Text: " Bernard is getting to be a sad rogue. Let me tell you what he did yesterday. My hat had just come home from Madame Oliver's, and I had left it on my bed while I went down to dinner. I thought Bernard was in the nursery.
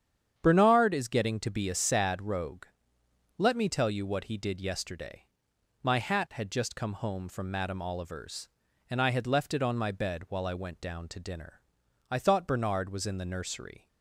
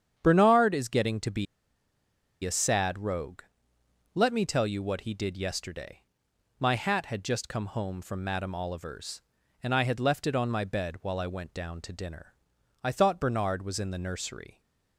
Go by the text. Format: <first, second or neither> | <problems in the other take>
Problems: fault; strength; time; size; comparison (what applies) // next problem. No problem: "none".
first | starts louder than the rest; strong; until 1.2 s; 8.5 dB; strong in the first // pauses between "be" and "a"; at 1.4 s; 0.98 s long